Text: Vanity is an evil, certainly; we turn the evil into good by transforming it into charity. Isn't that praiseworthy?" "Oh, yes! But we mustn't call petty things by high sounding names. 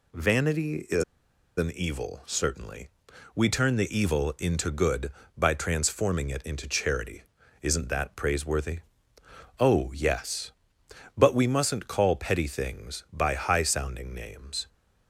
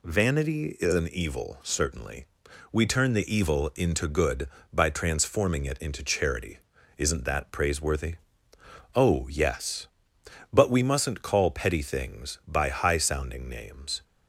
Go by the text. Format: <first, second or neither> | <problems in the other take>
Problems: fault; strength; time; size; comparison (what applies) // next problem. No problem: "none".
second | pauses between "is" and "an"; noticeable; at 1.0 s; 0.54 s long